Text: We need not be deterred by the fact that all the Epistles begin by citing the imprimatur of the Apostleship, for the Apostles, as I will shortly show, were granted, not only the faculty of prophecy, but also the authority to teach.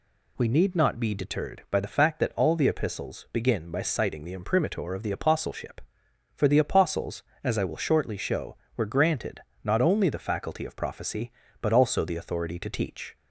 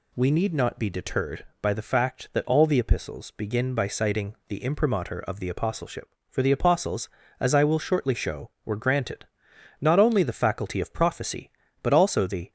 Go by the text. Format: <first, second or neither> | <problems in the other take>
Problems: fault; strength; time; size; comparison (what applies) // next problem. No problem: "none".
first | stops before "authority to teach"; at 12.4 s